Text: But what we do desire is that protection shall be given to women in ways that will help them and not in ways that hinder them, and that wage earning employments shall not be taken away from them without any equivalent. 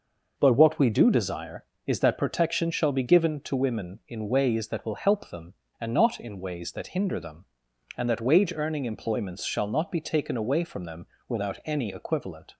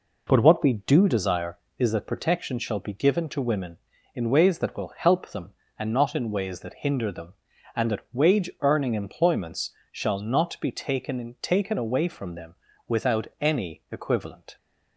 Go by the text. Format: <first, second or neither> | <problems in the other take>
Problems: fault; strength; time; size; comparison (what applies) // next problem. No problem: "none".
first | pauses between "employments" and "shall"; slight; at 9.7 s; 0.22 s long // says "taken" twice; at 11.4 s // pauses between "them" and "without"; slight; at 12.5 s; 0.34 s long; slight in the first